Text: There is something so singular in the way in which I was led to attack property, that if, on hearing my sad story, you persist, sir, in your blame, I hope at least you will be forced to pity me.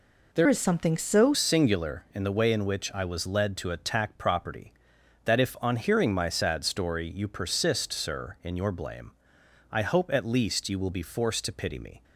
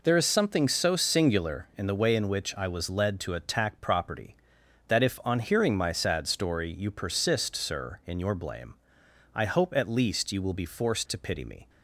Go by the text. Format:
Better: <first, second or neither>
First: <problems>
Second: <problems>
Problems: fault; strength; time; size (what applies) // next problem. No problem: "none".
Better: second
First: changes voice from "is" to "so"; from 0.4 to 1.3 s; 0.9 s long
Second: none